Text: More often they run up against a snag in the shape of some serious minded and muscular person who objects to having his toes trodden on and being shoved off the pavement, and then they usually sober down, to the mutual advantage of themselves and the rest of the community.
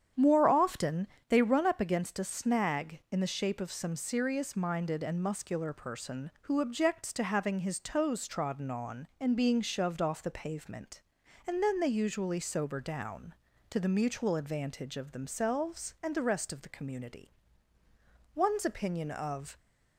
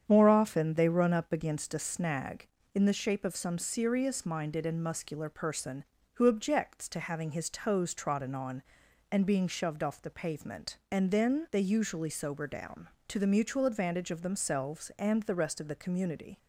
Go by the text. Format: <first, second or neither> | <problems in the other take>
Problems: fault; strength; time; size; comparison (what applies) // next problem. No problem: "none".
second | starts louder than the rest; strong; until 1.3 s; 9 dB; strong in the second // pauses between "often" and "they"; slight; at 1.0 s; 0.22 s long // goes on to say "One's opinion of"; noticeable; from 18.3 s on; 1.2 s long